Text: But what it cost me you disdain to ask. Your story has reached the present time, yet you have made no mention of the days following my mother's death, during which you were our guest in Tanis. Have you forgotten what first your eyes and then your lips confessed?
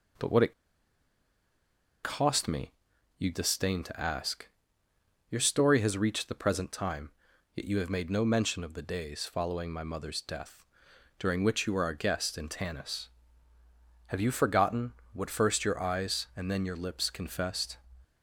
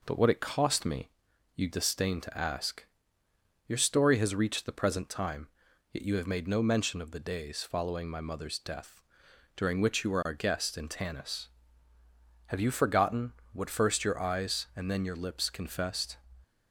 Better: second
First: pauses between "it" and "cost"; strong; at 0.5 s; 1.5 s long // pauses between "me" and "you"; noticeable; at 2.7 s; 0.46 s long // pauses between "forgotten" and "what"; slight; at 14.9 s; 0.22 s long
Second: pauses between "me" and "you"; noticeable; at 1.0 s; 0.46 s long // pauses between "forgotten" and "what"; slight; at 13.3 s; 0.22 s long

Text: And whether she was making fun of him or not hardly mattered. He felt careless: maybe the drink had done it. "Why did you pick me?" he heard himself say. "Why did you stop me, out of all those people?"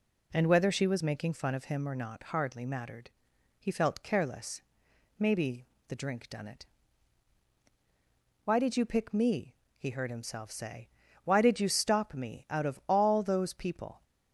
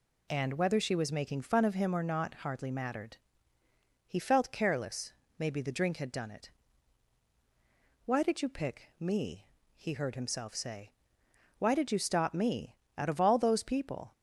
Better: second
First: pauses between "maybe" and "the"; slight; at 5.6 s; 0.24 s long // skips "had"; at 6.2 s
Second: none

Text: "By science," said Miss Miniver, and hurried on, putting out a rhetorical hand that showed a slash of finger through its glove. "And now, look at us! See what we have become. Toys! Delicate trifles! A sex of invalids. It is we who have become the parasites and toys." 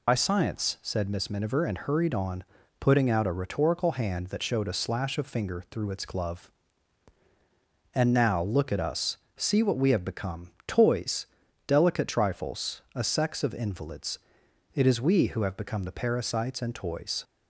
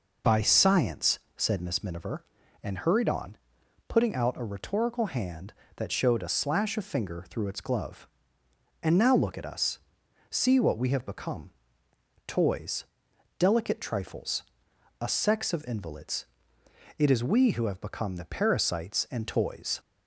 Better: second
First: loses the start of "By"; at 0.0 s; 55 ms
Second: none

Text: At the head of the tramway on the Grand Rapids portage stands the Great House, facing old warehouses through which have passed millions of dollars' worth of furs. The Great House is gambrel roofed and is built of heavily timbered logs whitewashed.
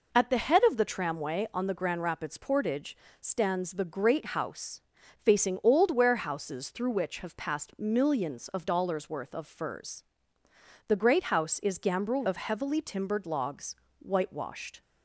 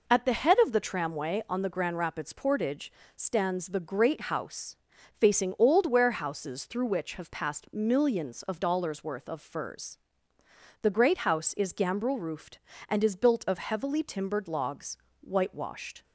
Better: second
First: pauses between "portage" and "stands"; slight; at 2.9 s; 0.24 s long // skips "roofed and is built"; at 12.2 s // pauses between "logs" and "whitewashed"; slight; at 13.7 s; 0.24 s long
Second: pauses between "portage" and "stands"; slight; at 2.9 s; 0.24 s long // pauses between "logs" and "whitewashed"; slight; at 14.9 s; 0.24 s long

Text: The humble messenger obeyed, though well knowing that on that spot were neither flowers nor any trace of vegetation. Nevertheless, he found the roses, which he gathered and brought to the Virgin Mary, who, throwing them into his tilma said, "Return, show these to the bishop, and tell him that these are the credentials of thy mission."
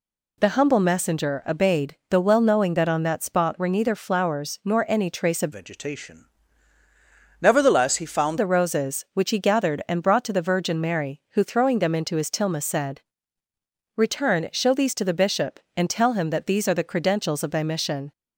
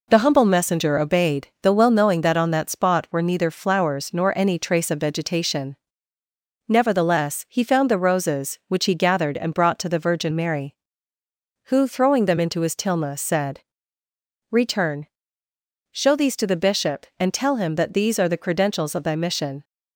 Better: second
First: changes voice from "vegetation" to "found"; from 5.5 to 8.3 s; 2.8 s long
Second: none

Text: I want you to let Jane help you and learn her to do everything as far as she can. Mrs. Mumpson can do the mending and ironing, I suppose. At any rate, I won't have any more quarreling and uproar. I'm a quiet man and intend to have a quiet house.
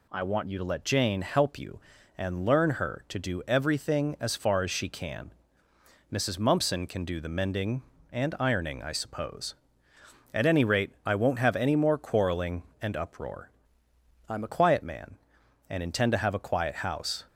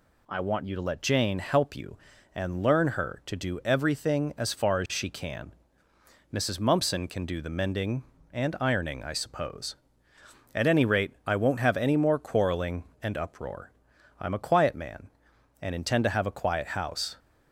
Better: second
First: changes voice from "I'm" to "a"; from 14.2 to 14.4 s; 0.2 s long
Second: none

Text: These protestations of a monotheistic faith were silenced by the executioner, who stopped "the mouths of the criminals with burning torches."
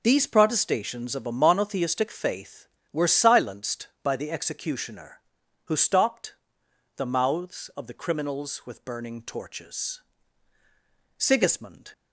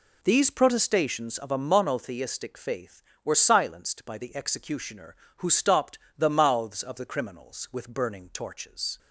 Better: second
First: pauses between "stopped" and "the"; noticeable; at 6.3 s; 0.64 s long // goes on to say "Sigismund"; noticeable; from 11.1 s on; 0.74 s long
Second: pauses between "stopped" and "the"; slight; at 5.9 s; 0.20 s long

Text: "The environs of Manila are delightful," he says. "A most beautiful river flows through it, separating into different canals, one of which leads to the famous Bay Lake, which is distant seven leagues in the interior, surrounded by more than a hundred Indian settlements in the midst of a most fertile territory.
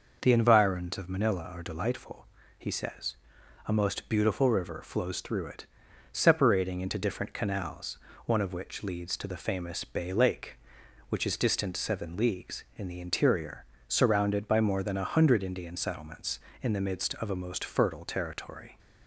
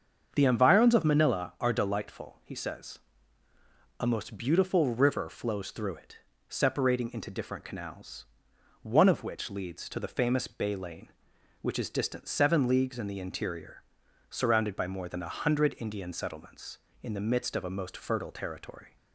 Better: first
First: none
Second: starts louder than the rest; until 1.3 s; 7 dB // says "Lane" for "Lake"; at 10.7 s

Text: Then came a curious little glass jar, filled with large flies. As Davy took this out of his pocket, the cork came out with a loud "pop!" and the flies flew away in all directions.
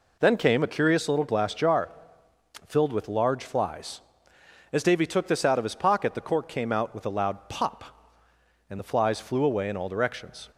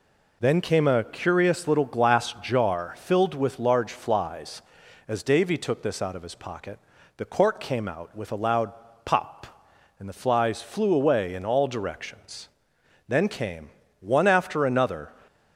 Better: first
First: none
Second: pauses between "loud" and "pop"; slight; at 8.7 s; 0.32 s long // goes on to say "Then came one after another"; strong; from 13.0 s on; 2.0 s long

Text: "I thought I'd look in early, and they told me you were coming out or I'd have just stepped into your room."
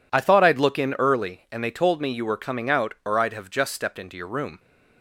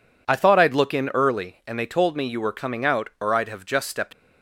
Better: first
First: none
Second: stops before "into your room"; at 4.1 s

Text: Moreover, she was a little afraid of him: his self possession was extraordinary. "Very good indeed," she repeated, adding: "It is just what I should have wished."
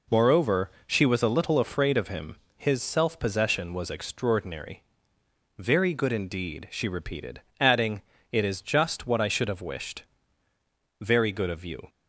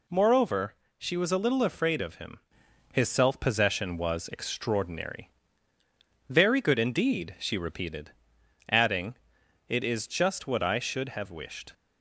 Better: second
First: goes on to say "Very good of you"; noticeable; from 10.9 s on; 0.92 s long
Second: none

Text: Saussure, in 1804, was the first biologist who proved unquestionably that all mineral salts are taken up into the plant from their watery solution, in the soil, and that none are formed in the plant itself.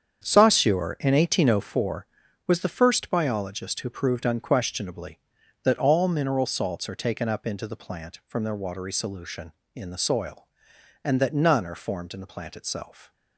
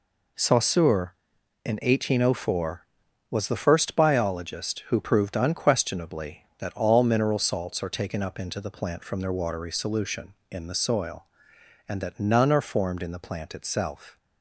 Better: second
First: starts louder than the rest; strong; until 1.7 s; 8 dB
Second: none

